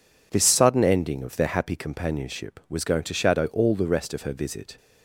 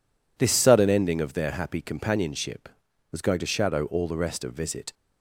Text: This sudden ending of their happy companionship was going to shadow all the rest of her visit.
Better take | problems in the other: first | skips "her"; at 4.5 s

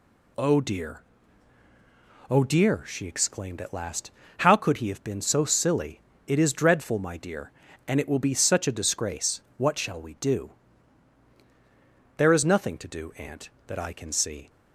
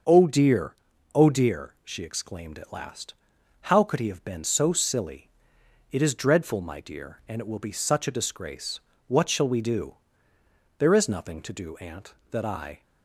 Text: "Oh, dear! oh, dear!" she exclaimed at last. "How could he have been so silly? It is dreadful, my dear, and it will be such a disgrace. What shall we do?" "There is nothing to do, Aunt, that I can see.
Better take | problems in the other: first | starts louder than the rest; until 1.4 s; 6.5 dB // stops before "can see"; at 12.8 s

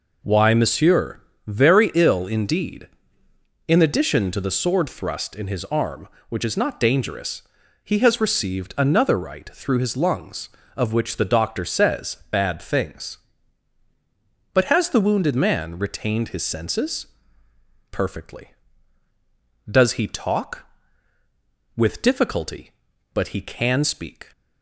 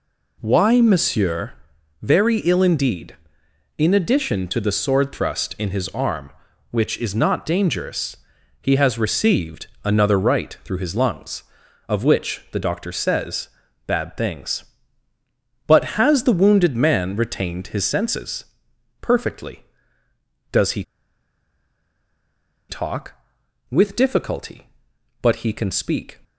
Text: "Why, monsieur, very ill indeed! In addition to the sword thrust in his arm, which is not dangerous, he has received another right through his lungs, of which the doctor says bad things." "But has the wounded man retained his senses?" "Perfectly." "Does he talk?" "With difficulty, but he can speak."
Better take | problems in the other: first | pauses between "received" and "another"; slight; at 9.6 s; 0.16 s long // pauses between "says" and "bad"; slight; at 13.4 s; 0.36 s long // pauses between "he" and "talk"; strong; at 20.8 s; 1.8 s long

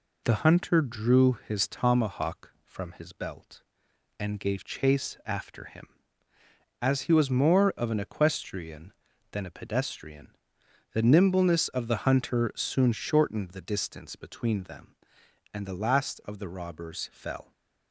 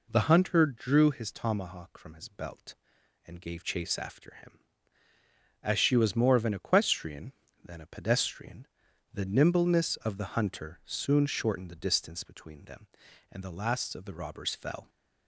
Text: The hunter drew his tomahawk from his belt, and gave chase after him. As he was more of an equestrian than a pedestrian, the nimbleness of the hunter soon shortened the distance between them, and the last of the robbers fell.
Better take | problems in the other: first | says "she" for "he"; at 5.7 s

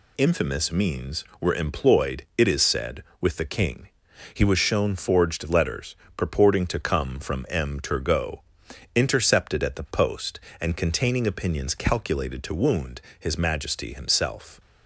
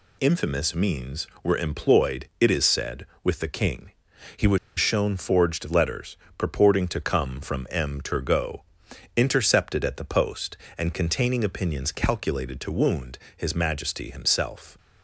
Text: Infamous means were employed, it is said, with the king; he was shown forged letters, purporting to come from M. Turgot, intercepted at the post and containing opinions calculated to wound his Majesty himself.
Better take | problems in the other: first | pauses between "was" and "shown"; slight; at 4.5 s; 0.20 s long // pauses between "wound" and "his"; slight; at 13.1 s; 0.18 s long; slight in the first

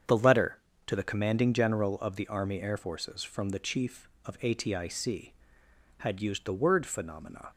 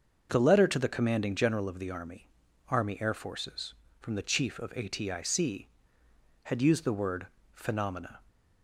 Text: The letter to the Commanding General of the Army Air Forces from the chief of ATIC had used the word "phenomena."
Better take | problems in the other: first | starts louder than the rest; until 1.3 s; 6.5 dB; strong in the first // says "Army" twice; at 2.6 s // pauses between "word" and "phenomena"; slight; at 7.2 s; 0.26 s long

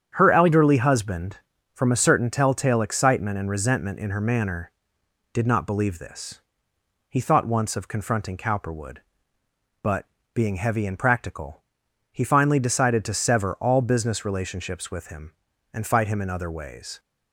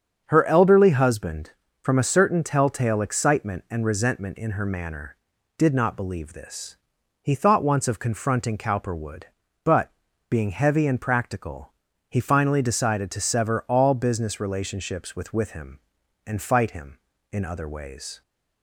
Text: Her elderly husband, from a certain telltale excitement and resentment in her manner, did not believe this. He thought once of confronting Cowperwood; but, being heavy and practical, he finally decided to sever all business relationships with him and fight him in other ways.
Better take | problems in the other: first | starts louder than the rest; until 1.2 s; 7 dB; strong in the first // says "with" twice; at 15.3 s

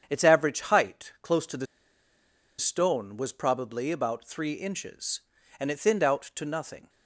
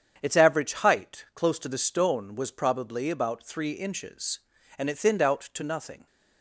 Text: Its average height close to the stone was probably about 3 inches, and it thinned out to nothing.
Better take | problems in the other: second | starts louder than the rest; strong; until 1.1 s; 8 dB; strong in the second // pauses between "the" and "stone"; noticeable; at 1.6 s; 0.93 s long

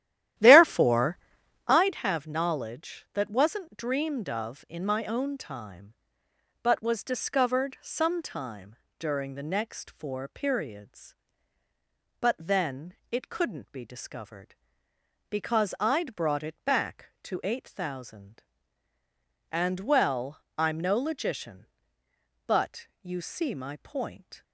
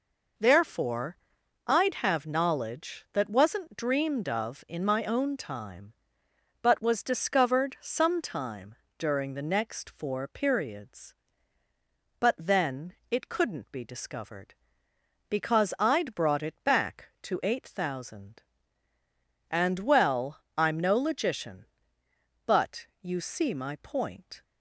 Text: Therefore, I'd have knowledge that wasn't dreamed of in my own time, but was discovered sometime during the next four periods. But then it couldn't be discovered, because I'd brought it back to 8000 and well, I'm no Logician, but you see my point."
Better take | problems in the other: second | starts louder than the rest; strong; until 1.9 s; 12.5 dB // pauses between "sometime" and "during"; slight; at 8.7 s; 0.24 s long; slight in the second // pauses between "then" and "it"; slight; at 12.9 s; 0.18 s long; slight in the second

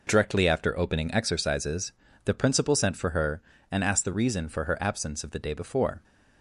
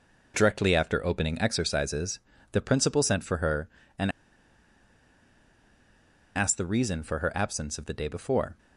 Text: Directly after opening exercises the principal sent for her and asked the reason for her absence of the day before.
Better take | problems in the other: first | pauses between "exercises" and "the"; slight; at 2.1 s; 0.32 s long; slight in the first // pauses between "and" and "asked"; strong; at 4.1 s; 2.2 s long

